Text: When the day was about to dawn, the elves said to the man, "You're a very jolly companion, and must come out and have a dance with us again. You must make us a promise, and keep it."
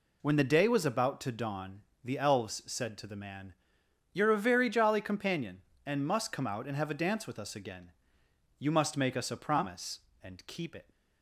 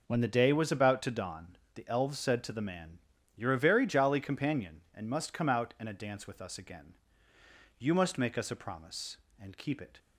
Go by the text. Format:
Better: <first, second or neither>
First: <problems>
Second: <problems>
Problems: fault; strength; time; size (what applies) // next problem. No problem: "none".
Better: first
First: none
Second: skips "have"; at 5.8 s